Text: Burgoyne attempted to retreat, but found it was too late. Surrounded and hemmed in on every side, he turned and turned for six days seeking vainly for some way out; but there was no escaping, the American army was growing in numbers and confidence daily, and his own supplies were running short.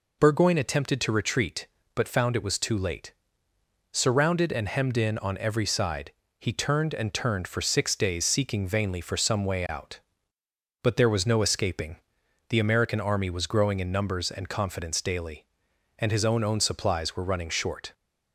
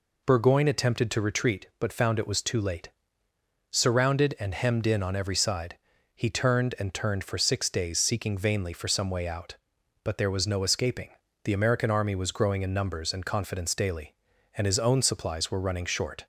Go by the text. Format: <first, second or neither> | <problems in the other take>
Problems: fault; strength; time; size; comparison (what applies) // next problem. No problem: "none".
second | says "own" twice; at 16.4 s